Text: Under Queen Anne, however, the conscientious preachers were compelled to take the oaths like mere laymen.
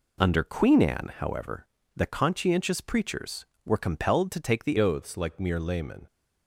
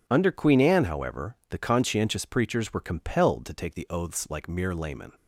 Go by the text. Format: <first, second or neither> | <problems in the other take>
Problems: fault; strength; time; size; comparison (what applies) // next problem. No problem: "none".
second | changes voice at "oaths"; from 4.7 s on; 1.3 s long